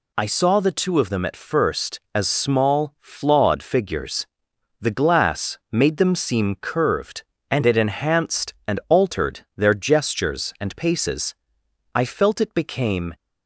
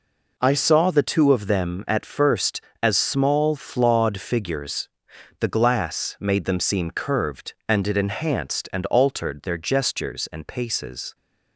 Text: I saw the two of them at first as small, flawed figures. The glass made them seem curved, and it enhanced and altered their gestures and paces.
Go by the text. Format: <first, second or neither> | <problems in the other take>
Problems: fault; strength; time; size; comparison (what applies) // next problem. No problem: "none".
second | pauses between "altered" and "their"; slight; at 9.4 s; 0.16 s long // goes on to say "I felt it became"; noticeable; from 11.9 s on; 1.2 s long